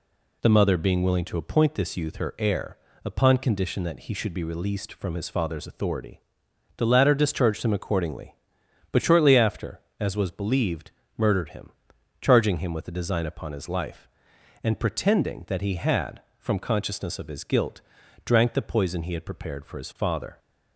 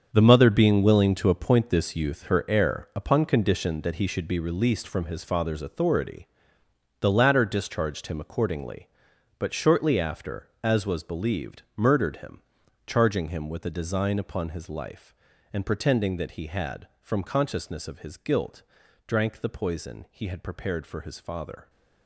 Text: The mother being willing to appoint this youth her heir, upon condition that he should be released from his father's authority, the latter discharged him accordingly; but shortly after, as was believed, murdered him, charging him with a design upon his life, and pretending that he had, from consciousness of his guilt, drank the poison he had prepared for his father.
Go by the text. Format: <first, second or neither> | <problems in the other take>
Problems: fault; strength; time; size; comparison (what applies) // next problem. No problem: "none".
first | gets quieter; strong; throughout; 12 dB